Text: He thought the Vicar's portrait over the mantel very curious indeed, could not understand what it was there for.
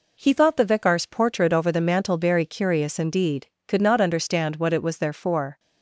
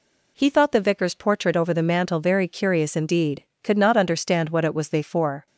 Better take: first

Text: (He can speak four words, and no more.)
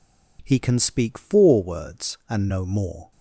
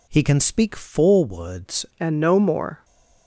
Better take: first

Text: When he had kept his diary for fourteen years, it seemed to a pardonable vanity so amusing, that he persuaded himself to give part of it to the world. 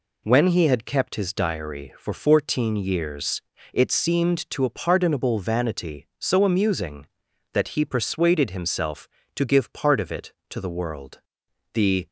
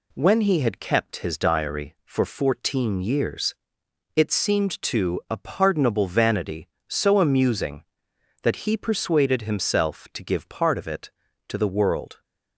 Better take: second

